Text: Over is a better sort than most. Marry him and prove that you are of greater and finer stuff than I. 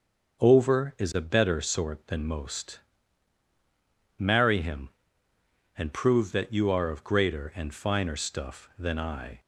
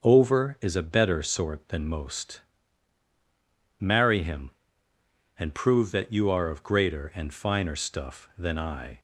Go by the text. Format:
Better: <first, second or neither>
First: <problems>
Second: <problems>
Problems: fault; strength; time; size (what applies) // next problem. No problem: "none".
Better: neither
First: starts louder than the rest; until 1.4 s; 6 dB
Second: starts louder than the rest; until 1.0 s; 6.5 dB